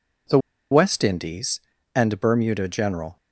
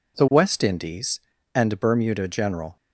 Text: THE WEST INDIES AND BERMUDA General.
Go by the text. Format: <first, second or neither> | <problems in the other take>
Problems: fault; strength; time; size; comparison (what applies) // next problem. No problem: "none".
second | pauses between "THE" and "WEST"; slight; at 0.3 s; 0.33 s long